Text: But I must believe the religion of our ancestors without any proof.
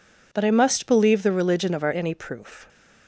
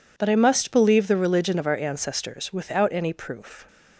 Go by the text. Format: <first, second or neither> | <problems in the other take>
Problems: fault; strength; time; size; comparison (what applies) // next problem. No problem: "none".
second | skips "ancestors without"; at 1.9 s